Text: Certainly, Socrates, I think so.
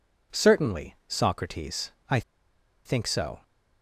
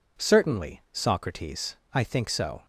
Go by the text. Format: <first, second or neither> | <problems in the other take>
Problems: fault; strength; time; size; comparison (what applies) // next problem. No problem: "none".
second | pauses between "I" and "think"; noticeable; at 2.2 s; 0.64 s long